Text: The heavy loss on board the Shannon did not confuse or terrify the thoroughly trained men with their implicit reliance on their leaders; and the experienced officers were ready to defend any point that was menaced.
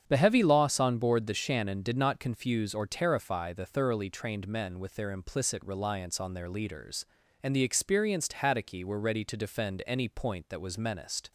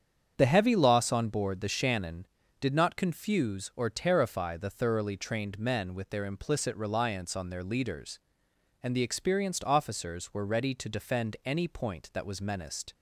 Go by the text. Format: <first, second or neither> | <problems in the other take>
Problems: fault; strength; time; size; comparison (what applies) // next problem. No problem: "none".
second | starts louder than the rest; strong; until 1.0 s; 8.5 dB; strong in the second // says "haddocky" for "officers"; at 8.3 s